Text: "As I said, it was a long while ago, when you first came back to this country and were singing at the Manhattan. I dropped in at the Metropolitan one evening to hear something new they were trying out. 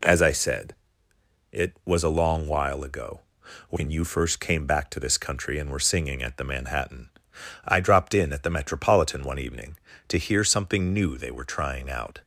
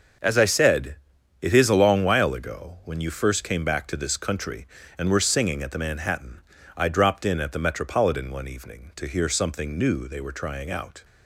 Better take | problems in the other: first | starts louder than the rest; until 1.6 s; 6 dB // says "is" for "was"; at 1.5 s

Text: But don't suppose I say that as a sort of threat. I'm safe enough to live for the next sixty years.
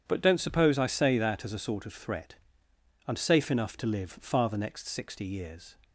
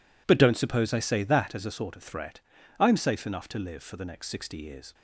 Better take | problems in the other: second | says "far" for "for"; at 4.1 s

